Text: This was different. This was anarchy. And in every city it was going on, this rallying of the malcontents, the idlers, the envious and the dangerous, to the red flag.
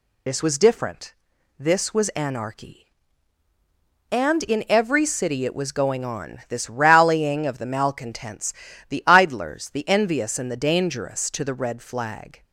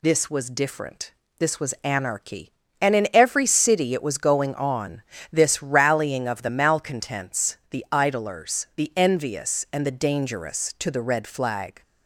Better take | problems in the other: second | loses the start of "This"; at 0.2 s; 40 ms

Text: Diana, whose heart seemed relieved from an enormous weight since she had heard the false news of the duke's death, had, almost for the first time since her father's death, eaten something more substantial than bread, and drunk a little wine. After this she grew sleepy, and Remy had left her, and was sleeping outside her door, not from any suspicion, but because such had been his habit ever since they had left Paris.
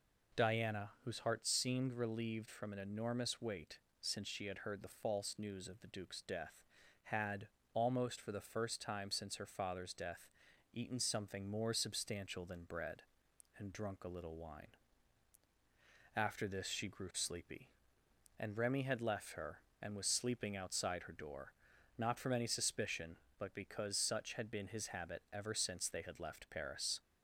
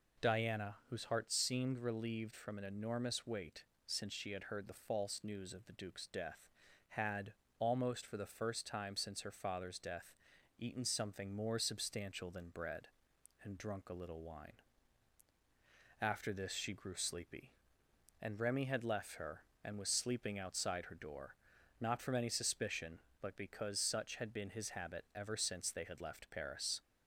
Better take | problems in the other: neither | pauses between "weight" and "since"; slight; the same in both

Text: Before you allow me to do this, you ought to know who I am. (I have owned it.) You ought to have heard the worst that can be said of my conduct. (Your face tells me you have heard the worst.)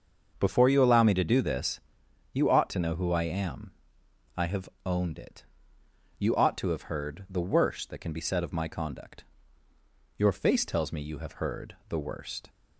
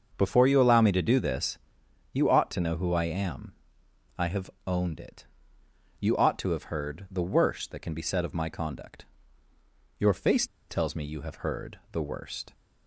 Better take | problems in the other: first | starts louder than the rest; until 1.1 s; 6.5 dB; also in the first // pauses between "have" and "owned"; slight; at 4.5 s; 0.16 s long; slight in the first // pauses between "face" and "tells"; slight; at 10.4 s; 0.24 s long

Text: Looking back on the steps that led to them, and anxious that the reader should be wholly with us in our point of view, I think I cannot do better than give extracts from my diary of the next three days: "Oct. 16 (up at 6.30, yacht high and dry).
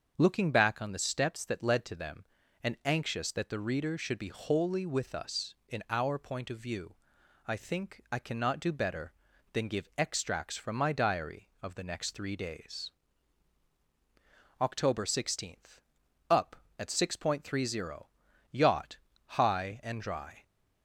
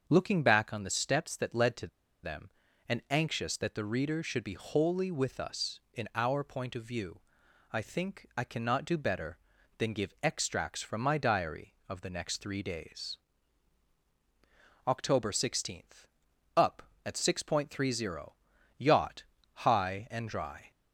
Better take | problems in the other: first | starts louder than the rest; until 1.0 s; 6.5 dB; also in the first // pauses between "to" and "them"; at 1.8 s; 0.36 s long // pauses between "yacht" and "high"; slight; at 19.2 s; 0.28 s long; slight in the first

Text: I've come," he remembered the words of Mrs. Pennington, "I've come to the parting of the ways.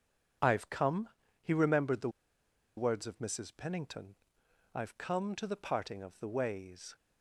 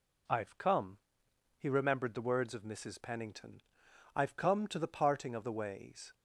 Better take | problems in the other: second | pauses between "the" and "words"; noticeable; at 2.0 s; 0.67 s long

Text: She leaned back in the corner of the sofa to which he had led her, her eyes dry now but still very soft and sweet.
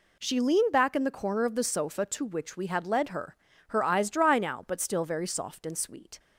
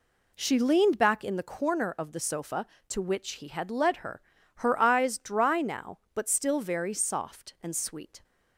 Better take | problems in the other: second | says "we" for "he"; at 2.5 s

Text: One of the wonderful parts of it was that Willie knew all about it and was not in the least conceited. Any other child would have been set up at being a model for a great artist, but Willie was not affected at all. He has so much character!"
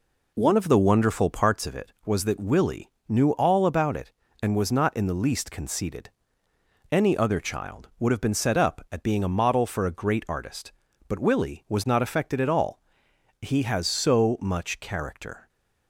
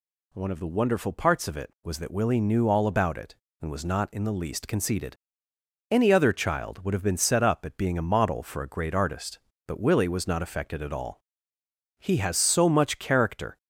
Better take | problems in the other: second | starts louder than the rest; until 1.7 s; 3.5 dB // pauses between "Willie" and "knew"; slight; at 2.8 s; 0.18 s long

